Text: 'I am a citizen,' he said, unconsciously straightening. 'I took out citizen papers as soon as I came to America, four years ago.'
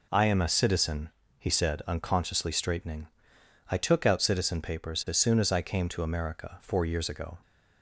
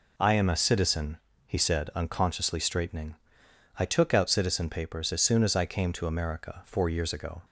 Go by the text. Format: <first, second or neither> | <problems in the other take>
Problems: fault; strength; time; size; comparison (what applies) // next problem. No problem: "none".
neither | none